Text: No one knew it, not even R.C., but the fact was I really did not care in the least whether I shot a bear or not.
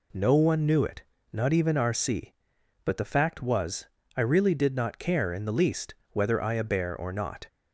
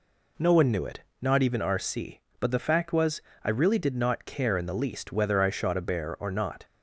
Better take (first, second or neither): second